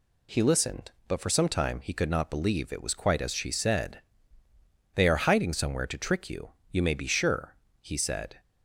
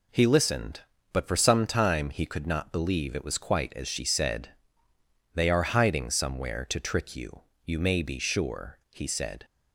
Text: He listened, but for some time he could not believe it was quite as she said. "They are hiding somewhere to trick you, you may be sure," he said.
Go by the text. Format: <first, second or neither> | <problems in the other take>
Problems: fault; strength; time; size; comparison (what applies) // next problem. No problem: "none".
neither | none